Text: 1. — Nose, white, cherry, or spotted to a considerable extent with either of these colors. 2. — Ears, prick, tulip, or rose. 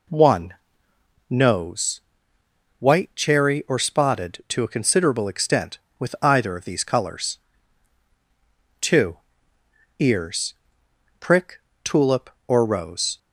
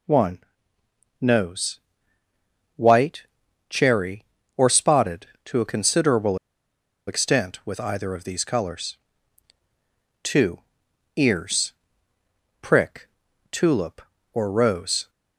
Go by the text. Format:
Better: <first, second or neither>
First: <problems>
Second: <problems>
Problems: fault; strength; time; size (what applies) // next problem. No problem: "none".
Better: first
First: none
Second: pauses between "considerable" and "extent"; noticeable; at 6.3 s; 0.71 s long